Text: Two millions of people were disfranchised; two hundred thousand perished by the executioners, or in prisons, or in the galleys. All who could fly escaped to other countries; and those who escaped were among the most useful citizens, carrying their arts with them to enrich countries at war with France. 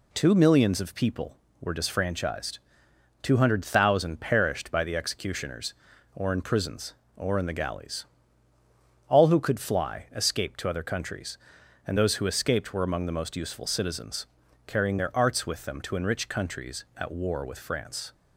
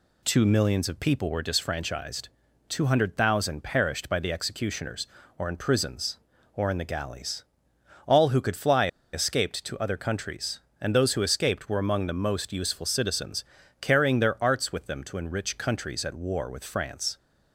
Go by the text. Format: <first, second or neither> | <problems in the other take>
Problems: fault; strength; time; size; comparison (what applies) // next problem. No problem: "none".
first | pauses between "fly" and "escaped"; slight; at 8.8 s; 0.25 s long